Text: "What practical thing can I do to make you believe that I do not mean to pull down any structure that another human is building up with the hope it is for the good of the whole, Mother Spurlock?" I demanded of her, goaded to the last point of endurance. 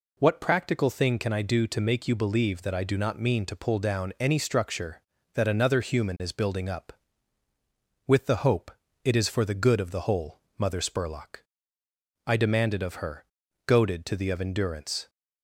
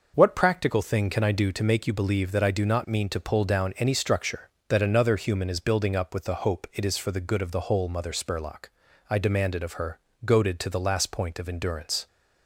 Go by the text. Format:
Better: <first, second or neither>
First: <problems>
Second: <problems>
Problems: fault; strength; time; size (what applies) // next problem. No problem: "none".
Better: second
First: pauses between "hope" and "it"; slight; at 8.7 s; 0.32 s long // skips "last point"; at 14.2 s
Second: none